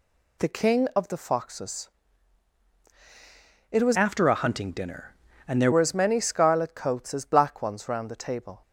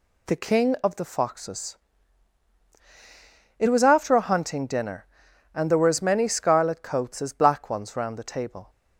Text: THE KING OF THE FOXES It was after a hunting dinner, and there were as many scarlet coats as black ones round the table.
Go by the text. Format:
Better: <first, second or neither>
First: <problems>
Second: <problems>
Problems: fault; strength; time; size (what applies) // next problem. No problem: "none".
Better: second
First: pauses between "FOXES" and "It"; strong; at 1.8 s; 1.8 s long // changes voice from "after" to "there"; from 3.9 to 5.7 s; 1.8 s long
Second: pauses between "FOXES" and "It"; strong; at 1.7 s; 1.8 s long